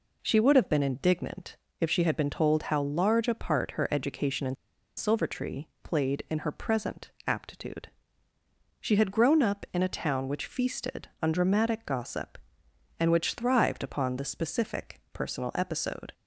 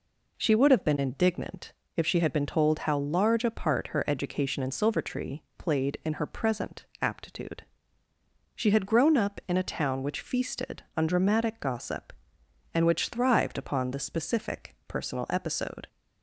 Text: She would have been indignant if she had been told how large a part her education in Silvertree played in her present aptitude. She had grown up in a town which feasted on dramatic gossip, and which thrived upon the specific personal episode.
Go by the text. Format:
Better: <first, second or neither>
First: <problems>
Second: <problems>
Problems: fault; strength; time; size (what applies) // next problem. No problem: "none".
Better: second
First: pauses between "indignant" and "if"; slight; at 1.5 s; 0.24 s long // pauses between "in" and "Silvertree"; at 4.5 s; 0.43 s long // pauses between "Silvertree" and "played"; slight; at 5.6 s; 0.16 s long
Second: pauses between "indignant" and "if"; slight; at 1.7 s; 0.24 s long // pauses between "Silvertree" and "played"; slight; at 5.4 s; 0.16 s long